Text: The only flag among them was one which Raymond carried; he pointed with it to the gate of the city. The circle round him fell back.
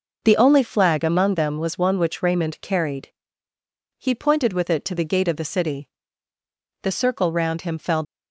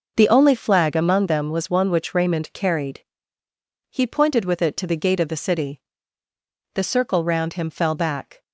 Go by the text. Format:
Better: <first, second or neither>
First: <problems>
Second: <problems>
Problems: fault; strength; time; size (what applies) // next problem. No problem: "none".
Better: second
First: stops before "back"; at 8.0 s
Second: none